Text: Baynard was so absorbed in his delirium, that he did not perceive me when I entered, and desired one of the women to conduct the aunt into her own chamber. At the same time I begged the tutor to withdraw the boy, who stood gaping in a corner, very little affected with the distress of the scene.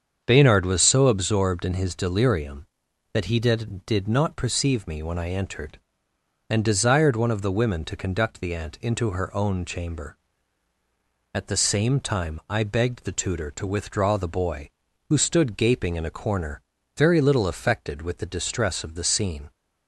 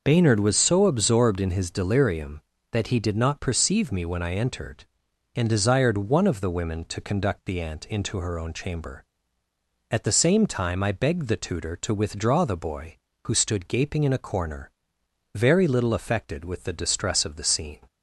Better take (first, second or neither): second